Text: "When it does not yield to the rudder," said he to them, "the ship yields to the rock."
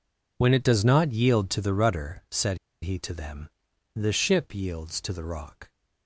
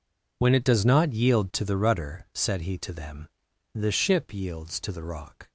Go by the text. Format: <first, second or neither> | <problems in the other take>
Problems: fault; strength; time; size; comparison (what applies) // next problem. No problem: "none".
second | pauses between "said" and "he"; slight; at 2.5 s; 0.25 s long